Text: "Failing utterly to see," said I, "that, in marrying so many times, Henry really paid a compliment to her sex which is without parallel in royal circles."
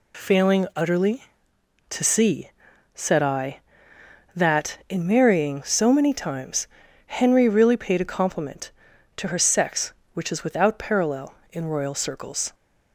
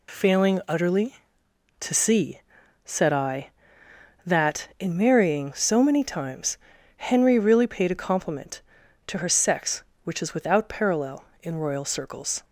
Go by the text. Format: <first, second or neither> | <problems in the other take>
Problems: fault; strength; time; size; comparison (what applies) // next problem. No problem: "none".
neither | none